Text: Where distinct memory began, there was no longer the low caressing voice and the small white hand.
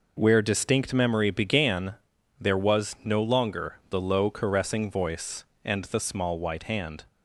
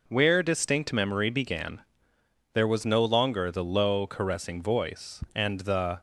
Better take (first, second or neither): first